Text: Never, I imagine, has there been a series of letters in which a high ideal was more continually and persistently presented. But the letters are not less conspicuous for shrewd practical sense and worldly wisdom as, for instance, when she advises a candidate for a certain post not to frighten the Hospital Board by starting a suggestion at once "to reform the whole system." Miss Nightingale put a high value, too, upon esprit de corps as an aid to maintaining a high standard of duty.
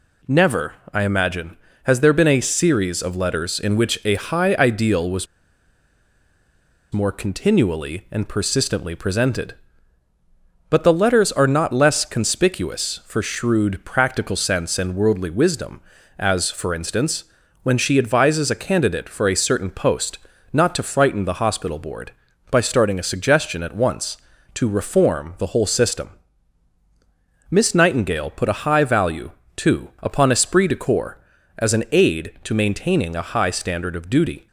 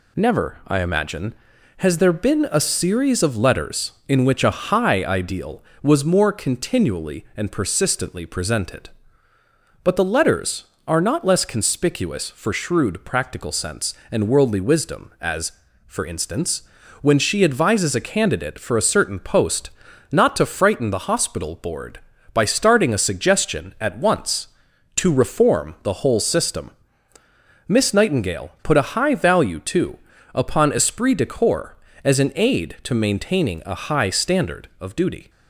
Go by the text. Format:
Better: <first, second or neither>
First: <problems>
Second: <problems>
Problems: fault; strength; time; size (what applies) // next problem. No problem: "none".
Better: second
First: pauses between "was" and "more"; strong; at 5.2 s; 1.6 s long // pauses between "post" and "not"; slight; at 20.1 s; 0.32 s long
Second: pauses between "post" and "not"; at 19.6 s; 0.42 s long